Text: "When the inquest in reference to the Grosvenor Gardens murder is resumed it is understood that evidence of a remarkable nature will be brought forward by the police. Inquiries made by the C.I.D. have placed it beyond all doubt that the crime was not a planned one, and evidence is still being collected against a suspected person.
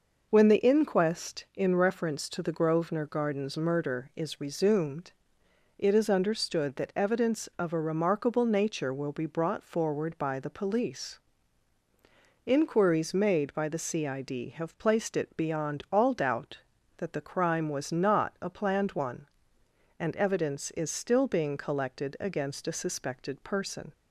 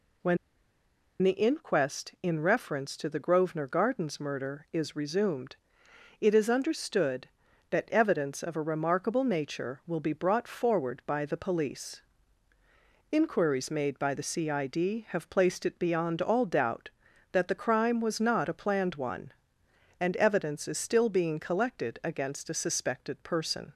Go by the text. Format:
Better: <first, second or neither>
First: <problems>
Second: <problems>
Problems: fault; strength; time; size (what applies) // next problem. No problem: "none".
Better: first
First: pauses between "resumed" and "it"; noticeable; at 5.1 s; 0.66 s long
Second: pauses between "When" and "the"; noticeable; at 0.3 s; 0.85 s long // pauses between "resumed" and "it"; noticeable; at 5.5 s; 0.66 s long